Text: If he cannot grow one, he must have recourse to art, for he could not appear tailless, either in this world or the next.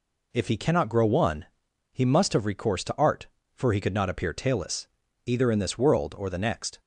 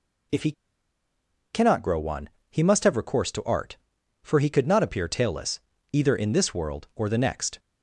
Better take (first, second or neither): first